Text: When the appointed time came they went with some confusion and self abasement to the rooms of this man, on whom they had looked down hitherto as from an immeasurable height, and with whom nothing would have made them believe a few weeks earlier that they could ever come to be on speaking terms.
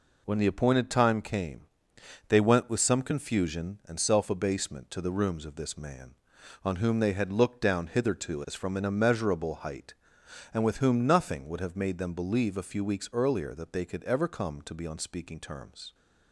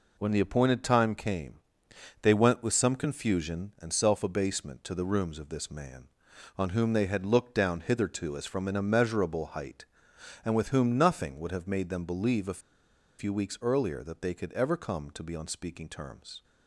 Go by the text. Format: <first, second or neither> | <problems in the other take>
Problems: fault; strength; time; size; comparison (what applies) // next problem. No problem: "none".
first | pauses between "came" and "they"; noticeable; at 1.5 s; 0.64 s long; noticeable in the first // pauses between "a" and "few"; noticeable; at 12.6 s; 0.57 s long